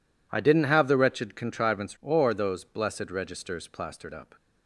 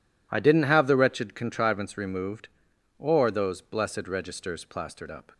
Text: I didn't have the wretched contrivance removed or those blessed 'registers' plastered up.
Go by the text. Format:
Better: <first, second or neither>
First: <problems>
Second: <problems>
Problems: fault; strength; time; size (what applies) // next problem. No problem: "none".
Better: second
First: skips "removed"; at 1.9 s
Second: none